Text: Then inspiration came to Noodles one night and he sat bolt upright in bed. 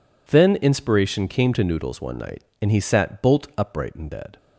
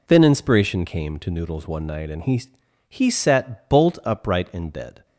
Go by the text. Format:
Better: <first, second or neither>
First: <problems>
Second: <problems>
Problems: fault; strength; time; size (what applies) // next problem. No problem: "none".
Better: first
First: none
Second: says "he" twice; at 2.8 s